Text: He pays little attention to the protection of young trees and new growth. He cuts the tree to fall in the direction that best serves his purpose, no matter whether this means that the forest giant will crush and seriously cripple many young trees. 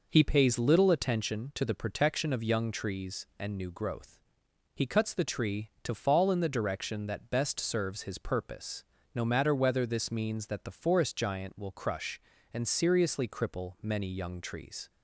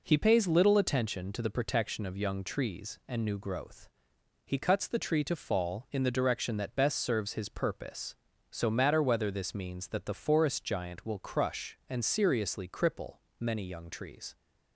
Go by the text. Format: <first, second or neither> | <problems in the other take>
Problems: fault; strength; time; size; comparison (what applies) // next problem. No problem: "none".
first | says "so" for "no"; at 8.4 s // pauses between "cripple" and "many"; slight; at 13.1 s; 0.24 s long